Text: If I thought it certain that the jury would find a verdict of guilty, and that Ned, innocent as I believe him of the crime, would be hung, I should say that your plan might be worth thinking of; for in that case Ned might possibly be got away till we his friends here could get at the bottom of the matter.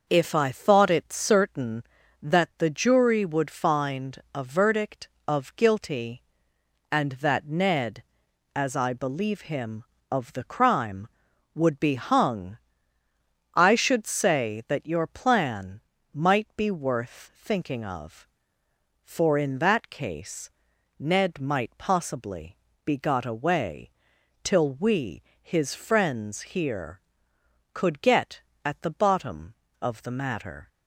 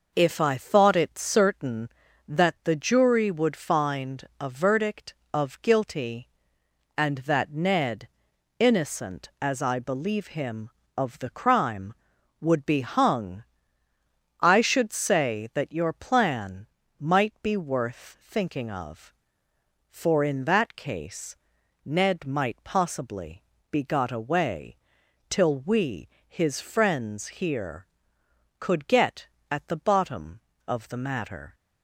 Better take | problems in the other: second | starts louder than the rest; noticeable; until 1.0 s; 6 dB // pauses between "find" and "a"; slight; at 4.1 s; 0.16 s long; slight in the second // skips "innocent"; at 8.2 s // pauses between "plan" and "might"; slight; at 15.8 s; 0.34 s long; slight in the second // pauses between "case" and "Ned"; noticeable; at 20.5 s; 0.50 s long; noticeable in the second // pauses between "possibly" and "be"; slight; at 22.5 s; 0.26 s long; slight in the second // pauses between "away" and "till"; noticeable; at 23.9 s; 0.54 s long; noticeable in the second // pauses between "we" and "his"; slight; at 25.2 s; 0.22 s long; slight in the second

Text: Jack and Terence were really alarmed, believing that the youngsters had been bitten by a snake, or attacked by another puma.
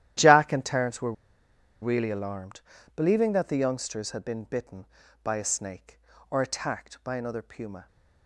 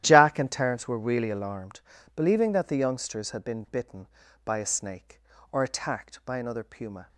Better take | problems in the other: second | starts louder than the rest; strong; until 1.8 s; 12.5 dB; strong in the second // pauses between "were" and "really"; noticeable; at 1.1 s; 0.69 s long

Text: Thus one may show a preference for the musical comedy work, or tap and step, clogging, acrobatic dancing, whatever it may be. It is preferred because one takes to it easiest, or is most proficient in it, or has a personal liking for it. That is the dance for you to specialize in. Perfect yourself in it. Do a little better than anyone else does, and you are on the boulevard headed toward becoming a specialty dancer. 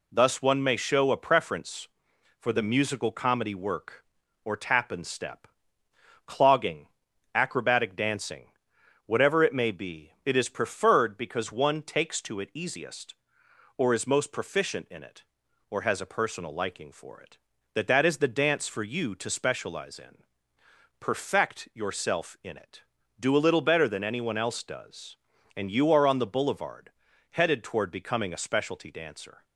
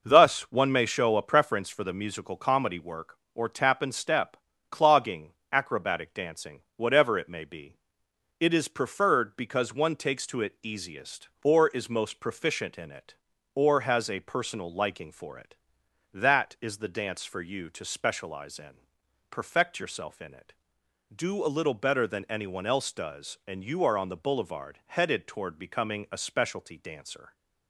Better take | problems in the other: second | says "That" twice; at 17.8 s // pauses between "boulevard" and "headed"; at 26.9 s; 0.40 s long

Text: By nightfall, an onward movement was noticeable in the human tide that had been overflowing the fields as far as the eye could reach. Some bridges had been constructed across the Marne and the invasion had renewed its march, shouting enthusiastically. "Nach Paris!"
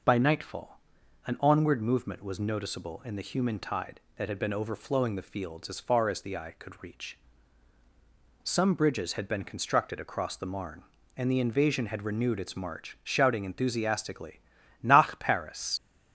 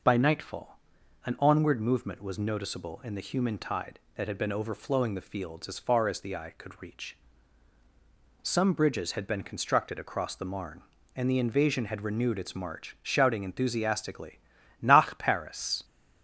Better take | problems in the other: second | leaves "Paris" unfinished; at 15.7 s; 80 ms

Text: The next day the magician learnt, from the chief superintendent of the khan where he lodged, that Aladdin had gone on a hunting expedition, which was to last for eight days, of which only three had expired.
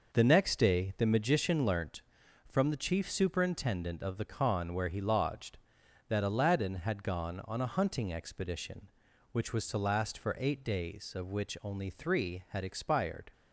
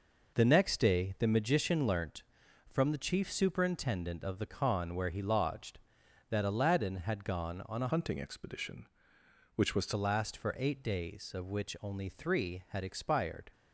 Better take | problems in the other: first | changes voice from "hunting" to "to"; from 7.9 to 9.9 s; 2.0 s long

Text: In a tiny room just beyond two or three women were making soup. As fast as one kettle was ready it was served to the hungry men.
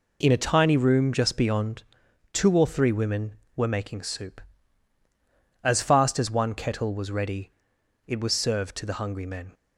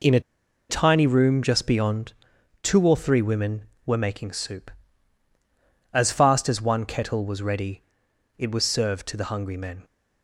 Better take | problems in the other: first | pauses between "a" and "tiny"; noticeable; at 0.2 s; 0.48 s long // pauses between "beyond" and "two"; noticeable; at 2.1 s; 0.50 s long; noticeable in the first // pauses between "ready" and "it"; noticeable; at 7.8 s; 0.52 s long; noticeable in the first

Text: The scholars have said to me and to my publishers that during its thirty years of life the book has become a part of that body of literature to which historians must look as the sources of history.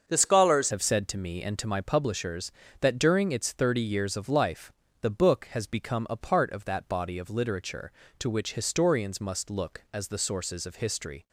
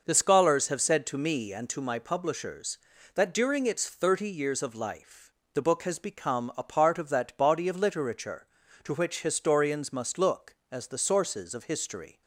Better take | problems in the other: second | starts louder than the rest; until 1.1 s; 6.5 dB // changes voice at "have"; from 0.7 s on; 10.5 s long // pauses between "life" and "the"; slight; at 4.7 s; 0.30 s long; slight in the second

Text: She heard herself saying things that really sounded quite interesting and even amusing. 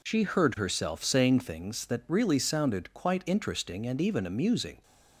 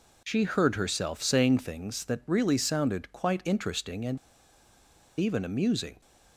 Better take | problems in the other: first | pauses between "and" and "even"; at 4.1 s; 1.0 s long

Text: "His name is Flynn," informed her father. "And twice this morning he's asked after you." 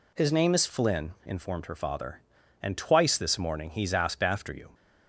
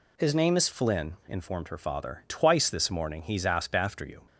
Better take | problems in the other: first | skips "And"; at 2.2 s

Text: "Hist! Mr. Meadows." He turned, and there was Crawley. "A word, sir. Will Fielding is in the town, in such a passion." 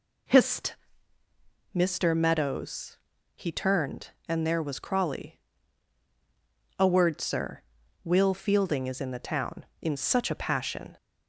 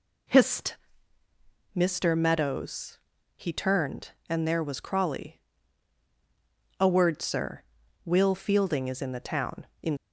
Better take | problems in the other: first | stops before "such a passion"; at 9.9 s

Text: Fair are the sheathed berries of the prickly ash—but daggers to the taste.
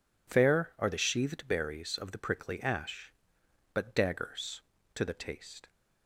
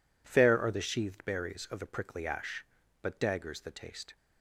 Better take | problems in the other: first | skips "to"; at 3.5 s

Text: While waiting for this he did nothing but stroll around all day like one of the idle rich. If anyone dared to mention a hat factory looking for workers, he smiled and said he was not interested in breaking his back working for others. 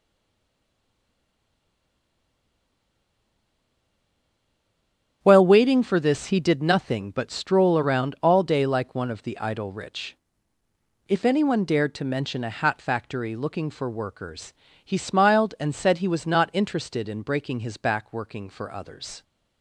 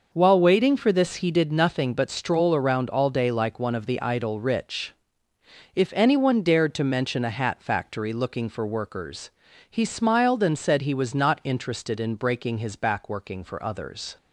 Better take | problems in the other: second | stays silent before the first word; strong; until 5.2 s; 5.2 s long // starts louder than the rest; strong; until 6.2 s; 8 dB

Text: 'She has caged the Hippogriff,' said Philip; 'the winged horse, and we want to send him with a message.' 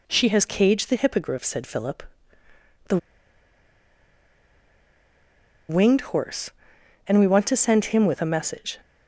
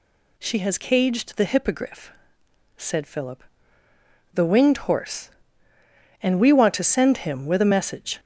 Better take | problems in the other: second | pauses between "the" and "winged"; strong; at 2.9 s; 2.7 s long

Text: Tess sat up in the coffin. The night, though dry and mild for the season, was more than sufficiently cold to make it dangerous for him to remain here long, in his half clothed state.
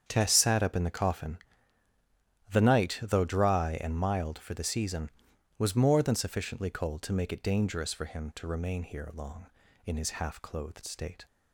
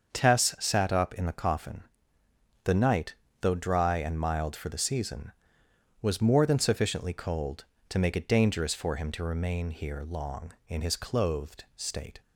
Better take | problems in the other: first | starts louder than the rest; until 1.1 s; 6.5 dB; strong in the first // skips "half"; at 10.9 s

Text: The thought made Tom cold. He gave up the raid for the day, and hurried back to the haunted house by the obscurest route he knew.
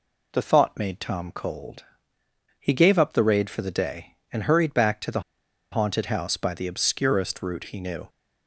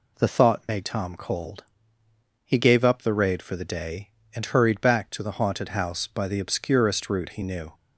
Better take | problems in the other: second | pauses between "the" and "haunted"; noticeable; at 5.2 s; 0.49 s long

